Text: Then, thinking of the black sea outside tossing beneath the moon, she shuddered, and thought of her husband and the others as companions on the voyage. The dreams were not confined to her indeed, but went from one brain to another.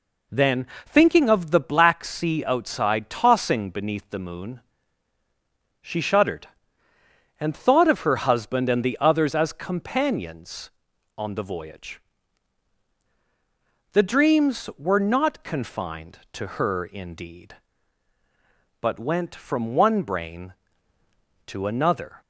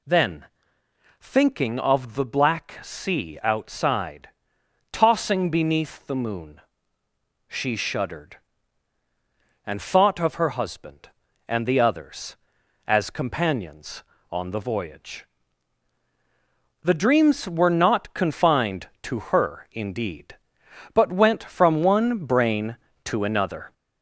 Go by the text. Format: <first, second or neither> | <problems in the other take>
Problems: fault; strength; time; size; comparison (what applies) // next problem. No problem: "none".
first | gets louder; slight; throughout; 3 dB // pauses between "outside" and "tossing"; noticeable; at 4.2 s; 0.62 s long